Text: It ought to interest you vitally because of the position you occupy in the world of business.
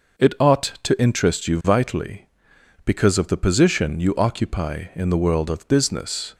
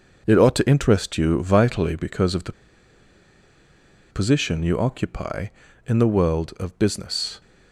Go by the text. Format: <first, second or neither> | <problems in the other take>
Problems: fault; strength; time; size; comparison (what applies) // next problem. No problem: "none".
first | pauses between "the" and "position"; strong; at 2.5 s; 1.5 s long